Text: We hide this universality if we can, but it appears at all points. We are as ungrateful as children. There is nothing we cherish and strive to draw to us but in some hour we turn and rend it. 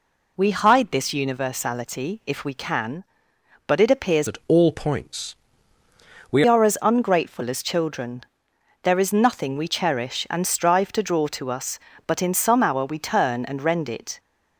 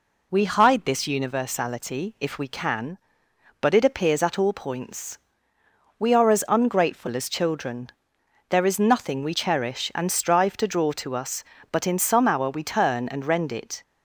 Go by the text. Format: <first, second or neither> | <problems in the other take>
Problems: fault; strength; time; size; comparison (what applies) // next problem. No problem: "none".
second | changes voice from "at" to "We"; from 4.2 to 6.4 s; 2.2 s long